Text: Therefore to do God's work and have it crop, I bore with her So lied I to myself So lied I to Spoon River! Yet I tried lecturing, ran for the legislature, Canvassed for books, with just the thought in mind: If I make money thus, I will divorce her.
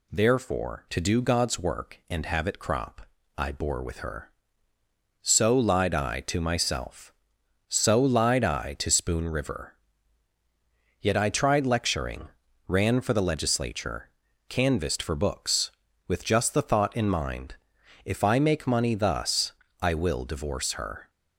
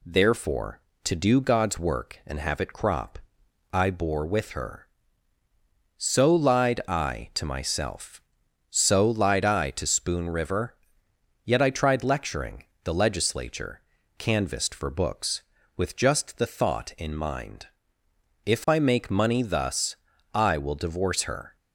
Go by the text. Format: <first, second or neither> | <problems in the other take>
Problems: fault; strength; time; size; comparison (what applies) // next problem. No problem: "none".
first | skips "ran for"; at 12.7 s